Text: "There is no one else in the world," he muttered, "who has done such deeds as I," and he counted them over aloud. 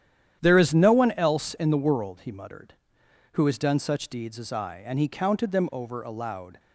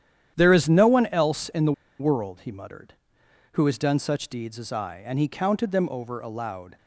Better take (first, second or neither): first